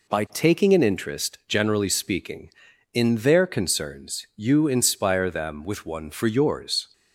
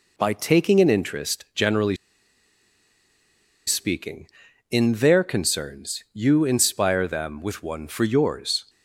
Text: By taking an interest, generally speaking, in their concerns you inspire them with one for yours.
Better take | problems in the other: first | pauses between "generally" and "speaking"; strong; at 1.9 s; 1.7 s long

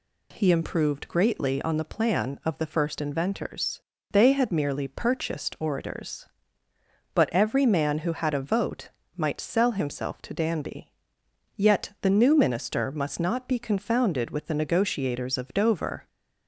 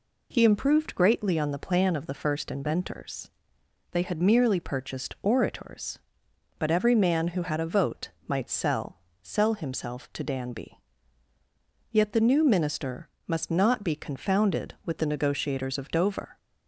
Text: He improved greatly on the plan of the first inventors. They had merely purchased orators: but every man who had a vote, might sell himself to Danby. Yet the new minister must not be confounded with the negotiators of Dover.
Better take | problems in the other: first | says "sell" twice; at 9.2 s // pauses between "minister" and "must"; slight; at 13.0 s; 0.18 s long

